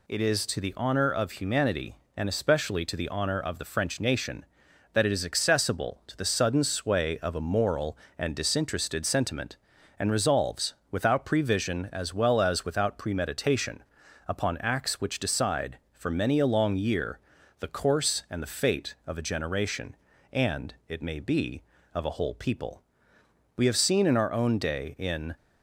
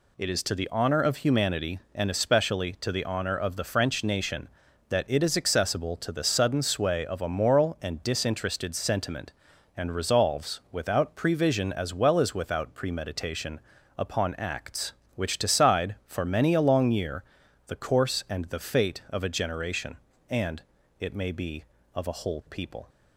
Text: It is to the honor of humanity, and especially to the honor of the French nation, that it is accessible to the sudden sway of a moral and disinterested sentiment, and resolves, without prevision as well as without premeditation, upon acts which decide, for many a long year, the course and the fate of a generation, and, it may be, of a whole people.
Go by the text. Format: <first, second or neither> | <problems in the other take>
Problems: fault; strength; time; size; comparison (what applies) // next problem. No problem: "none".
second | goes on to say "We have seen in our own day in"; strong; from 23.5 s on; 1.7 s long